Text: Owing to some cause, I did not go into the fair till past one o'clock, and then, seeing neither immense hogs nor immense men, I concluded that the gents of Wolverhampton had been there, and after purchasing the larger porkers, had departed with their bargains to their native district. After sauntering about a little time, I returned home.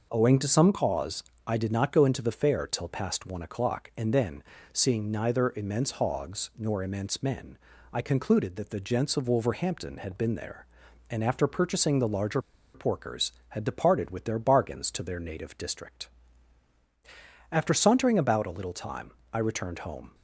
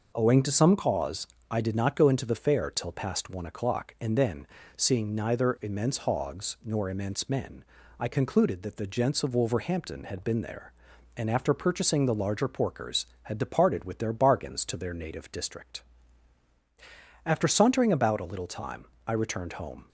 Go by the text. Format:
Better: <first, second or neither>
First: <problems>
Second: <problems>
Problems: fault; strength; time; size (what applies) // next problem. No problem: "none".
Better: second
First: pauses between "larger" and "porkers"; slight; at 12.4 s; 0.32 s long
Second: none